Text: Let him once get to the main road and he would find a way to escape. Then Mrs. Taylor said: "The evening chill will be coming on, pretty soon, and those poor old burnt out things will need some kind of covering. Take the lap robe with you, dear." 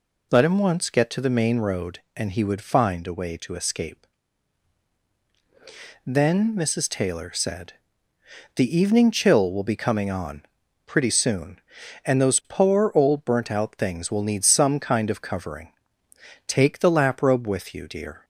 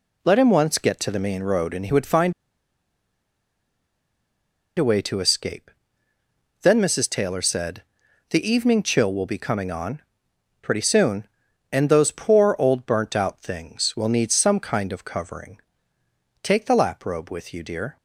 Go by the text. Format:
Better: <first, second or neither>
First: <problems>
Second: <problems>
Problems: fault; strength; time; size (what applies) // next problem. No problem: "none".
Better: first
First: none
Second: pauses between "find" and "a"; strong; at 2.3 s; 2.4 s long